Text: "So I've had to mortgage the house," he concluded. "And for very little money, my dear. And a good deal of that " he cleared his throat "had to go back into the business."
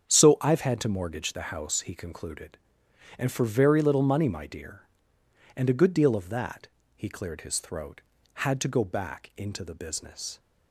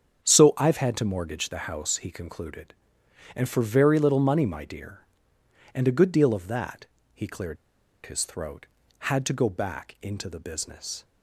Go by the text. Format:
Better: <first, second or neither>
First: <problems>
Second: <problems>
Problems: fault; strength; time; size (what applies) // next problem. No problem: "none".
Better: first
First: starts louder than the rest; strong; until 1.1 s; 8 dB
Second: starts louder than the rest; strong; until 1.2 s; 8 dB // pauses between "cleared" and "his"; noticeable; at 7.5 s; 0.49 s long